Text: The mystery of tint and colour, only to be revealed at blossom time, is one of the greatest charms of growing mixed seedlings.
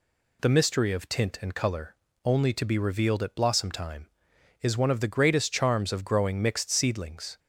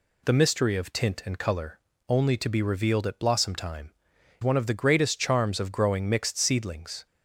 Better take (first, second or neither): first